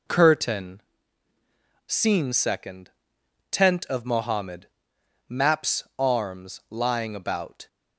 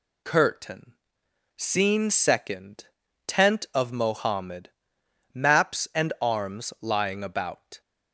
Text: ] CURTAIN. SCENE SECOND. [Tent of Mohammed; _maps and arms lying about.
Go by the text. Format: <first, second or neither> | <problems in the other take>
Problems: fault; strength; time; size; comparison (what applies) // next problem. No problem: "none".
second | skips "and"; at 5.9 s